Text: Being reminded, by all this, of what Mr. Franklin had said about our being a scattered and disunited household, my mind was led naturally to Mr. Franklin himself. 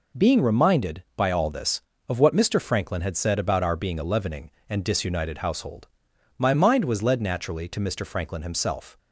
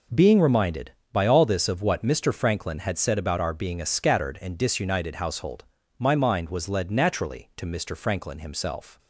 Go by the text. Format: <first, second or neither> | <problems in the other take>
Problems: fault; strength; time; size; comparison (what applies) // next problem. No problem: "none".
second | says "leavening" for "scattered"; at 4.0 s